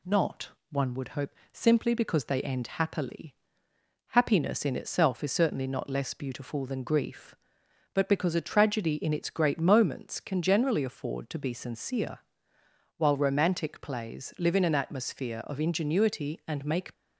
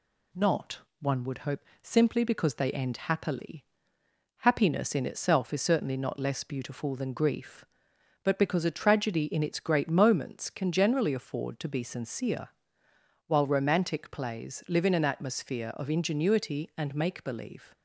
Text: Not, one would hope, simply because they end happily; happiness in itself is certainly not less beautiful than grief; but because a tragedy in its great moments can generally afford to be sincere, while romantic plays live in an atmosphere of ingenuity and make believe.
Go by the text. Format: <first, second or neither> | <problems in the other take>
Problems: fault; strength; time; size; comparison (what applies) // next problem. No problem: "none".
second | stops before "believe"; at 16.9 s